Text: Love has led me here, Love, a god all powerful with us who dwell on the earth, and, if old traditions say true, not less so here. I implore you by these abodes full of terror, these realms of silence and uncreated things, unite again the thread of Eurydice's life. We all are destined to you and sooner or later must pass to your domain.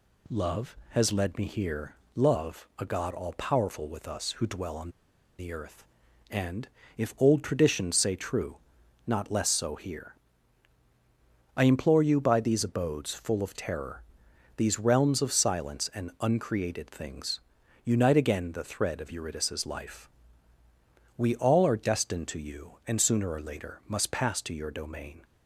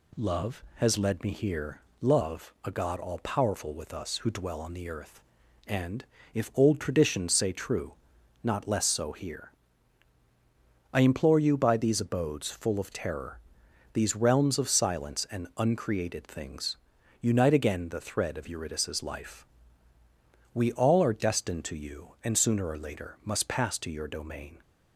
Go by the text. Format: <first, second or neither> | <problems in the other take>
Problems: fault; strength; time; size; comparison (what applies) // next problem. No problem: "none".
second | pauses between "on" and "the"; noticeable; at 4.8 s; 0.50 s long